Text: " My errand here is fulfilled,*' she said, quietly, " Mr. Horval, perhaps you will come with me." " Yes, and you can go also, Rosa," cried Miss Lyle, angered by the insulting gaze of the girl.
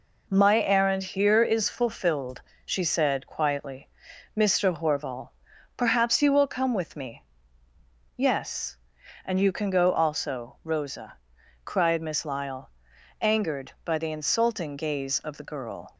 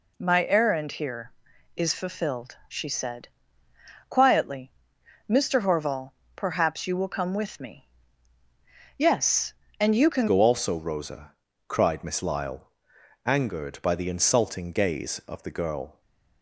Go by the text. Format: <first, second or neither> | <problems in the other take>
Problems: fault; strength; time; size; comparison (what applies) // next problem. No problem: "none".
first | changes voice at "go"; from 10.2 s on; 5.8 s long